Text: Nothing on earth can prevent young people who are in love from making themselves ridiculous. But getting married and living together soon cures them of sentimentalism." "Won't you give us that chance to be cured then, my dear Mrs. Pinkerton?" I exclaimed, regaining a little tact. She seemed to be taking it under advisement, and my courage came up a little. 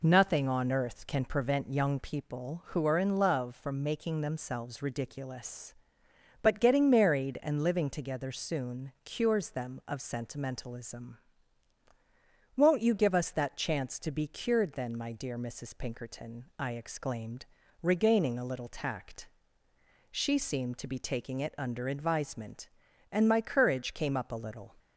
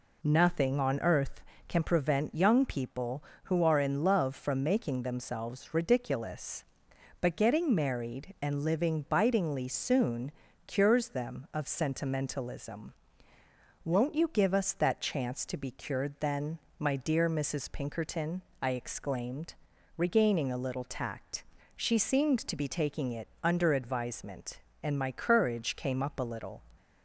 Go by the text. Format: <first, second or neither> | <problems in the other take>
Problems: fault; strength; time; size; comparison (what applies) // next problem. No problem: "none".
first | says "bitingly" for "together"; at 9.0 s // pauses between "soon" and "cures"; slight; at 10.3 s; 0.36 s long